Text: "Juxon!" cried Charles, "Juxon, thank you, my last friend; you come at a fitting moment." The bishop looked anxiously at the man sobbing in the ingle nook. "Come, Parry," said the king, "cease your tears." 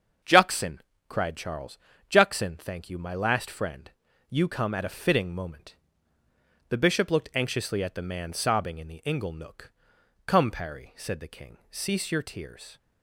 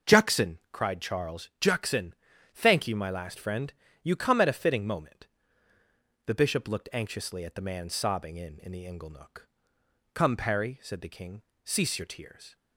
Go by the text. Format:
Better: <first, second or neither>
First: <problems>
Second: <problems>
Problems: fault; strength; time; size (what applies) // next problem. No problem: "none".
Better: first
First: starts louder than the rest; until 1.5 s; 7 dB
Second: starts louder than the rest; until 1.2 s; 6 dB // says "in" twice; at 8.5 s